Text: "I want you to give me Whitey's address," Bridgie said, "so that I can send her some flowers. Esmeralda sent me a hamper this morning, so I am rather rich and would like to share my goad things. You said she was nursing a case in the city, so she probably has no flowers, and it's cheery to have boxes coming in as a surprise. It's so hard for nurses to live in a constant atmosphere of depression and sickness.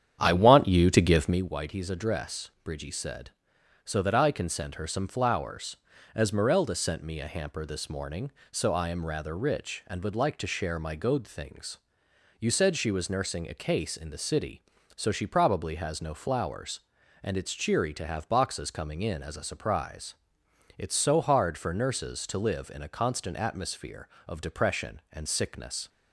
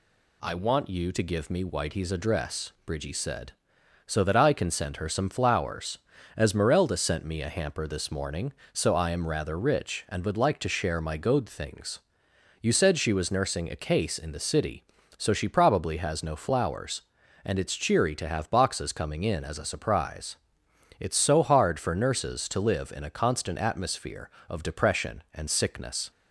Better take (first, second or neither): second